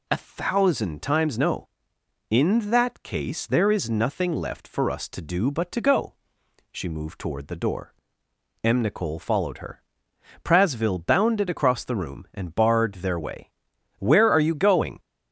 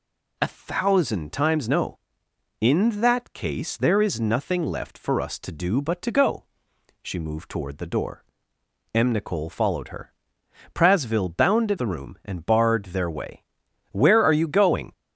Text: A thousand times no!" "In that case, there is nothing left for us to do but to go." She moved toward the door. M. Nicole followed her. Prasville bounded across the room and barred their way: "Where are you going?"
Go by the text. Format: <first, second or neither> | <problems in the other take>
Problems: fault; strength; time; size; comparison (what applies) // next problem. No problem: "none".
first | skips "across"; at 11.7 s